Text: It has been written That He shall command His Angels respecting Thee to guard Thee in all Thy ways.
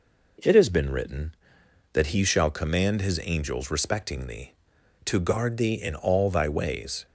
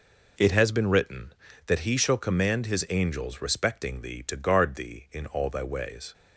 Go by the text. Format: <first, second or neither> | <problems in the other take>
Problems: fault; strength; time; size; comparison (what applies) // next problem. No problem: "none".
neither | none